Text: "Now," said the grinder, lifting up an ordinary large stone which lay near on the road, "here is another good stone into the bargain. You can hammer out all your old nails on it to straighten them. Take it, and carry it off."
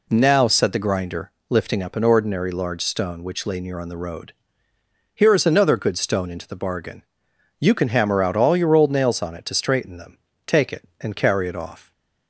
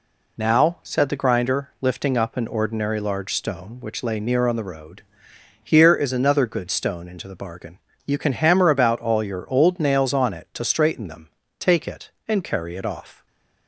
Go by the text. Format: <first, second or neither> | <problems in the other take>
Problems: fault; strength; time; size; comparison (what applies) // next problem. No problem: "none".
first | says "about" for "out"; at 8.6 s // stays silent after the last word; slight; from 13.1 s on; 0.5 s long